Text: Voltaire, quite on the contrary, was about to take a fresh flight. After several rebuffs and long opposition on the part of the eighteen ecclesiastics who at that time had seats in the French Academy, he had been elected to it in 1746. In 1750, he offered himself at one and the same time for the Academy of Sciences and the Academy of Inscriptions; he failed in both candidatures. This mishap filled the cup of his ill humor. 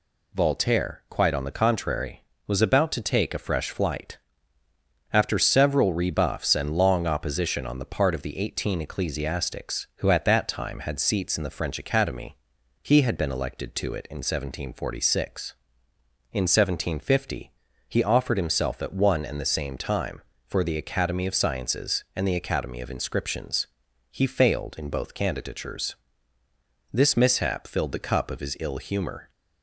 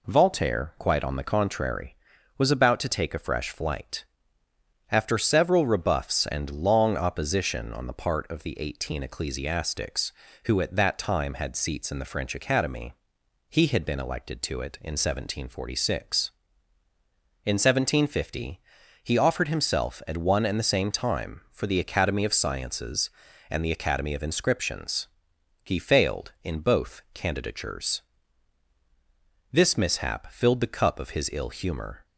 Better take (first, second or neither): neither